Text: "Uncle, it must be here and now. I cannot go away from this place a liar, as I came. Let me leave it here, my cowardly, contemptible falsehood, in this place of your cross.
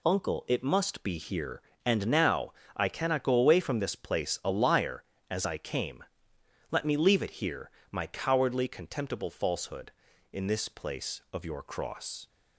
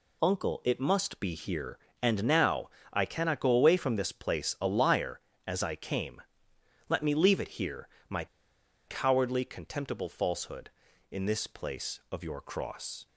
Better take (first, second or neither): first